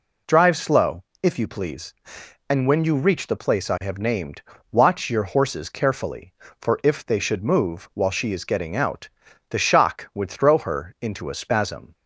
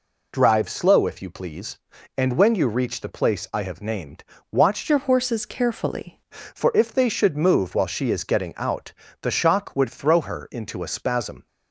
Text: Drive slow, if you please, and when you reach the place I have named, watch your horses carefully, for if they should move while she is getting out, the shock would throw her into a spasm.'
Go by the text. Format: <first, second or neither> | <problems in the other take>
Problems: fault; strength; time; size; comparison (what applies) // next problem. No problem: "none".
first | changes voice from "your" to "carefully"; from 4.8 to 6.1 s; 1.3 s long